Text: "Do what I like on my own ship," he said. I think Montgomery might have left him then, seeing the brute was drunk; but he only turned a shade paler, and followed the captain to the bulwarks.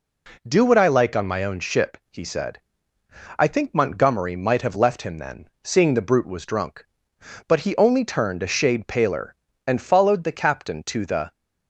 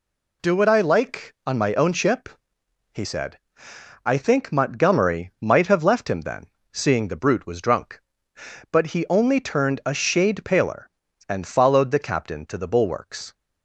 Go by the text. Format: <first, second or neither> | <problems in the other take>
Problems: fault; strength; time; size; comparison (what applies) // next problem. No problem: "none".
second | stops before "bulwarks"; at 11.3 s